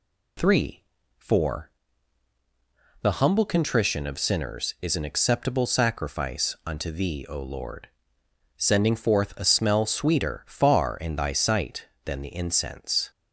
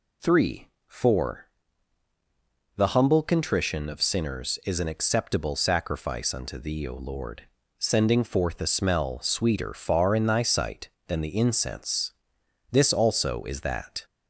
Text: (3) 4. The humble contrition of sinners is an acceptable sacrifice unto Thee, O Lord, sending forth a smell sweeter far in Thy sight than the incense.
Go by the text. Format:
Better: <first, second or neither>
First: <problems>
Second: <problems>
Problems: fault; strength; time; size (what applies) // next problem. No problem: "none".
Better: first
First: none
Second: goes on to say "This also is that"; from 12.6 s on; 1.3 s long